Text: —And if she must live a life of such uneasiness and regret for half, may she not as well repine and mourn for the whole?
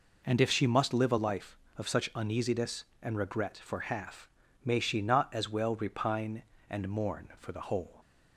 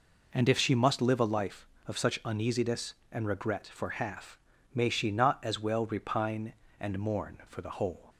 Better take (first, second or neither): neither